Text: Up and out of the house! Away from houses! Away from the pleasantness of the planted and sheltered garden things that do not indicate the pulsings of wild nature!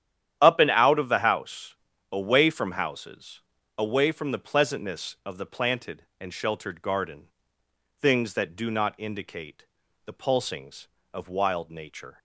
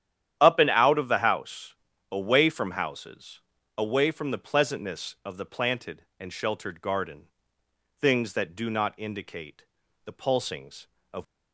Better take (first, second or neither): first